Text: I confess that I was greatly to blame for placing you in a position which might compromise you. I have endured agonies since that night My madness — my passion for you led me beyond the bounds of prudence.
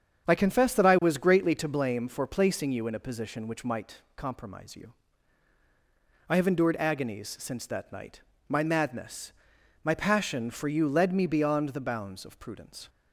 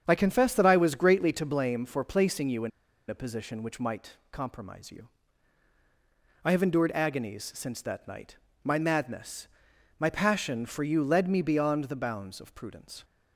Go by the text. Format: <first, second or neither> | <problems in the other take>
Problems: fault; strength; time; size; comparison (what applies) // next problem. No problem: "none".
first | starts louder than the rest; strong; until 1.0 s; 8 dB; strong in the first // pauses between "in" and "a"; at 2.7 s; 0.39 s long // pauses between "might" and "compromise"; slight; at 4.1 s; 0.16 s long; slight in the first // pauses between "night" and "My"; slight; at 8.3 s; 0.28 s long; slight in the first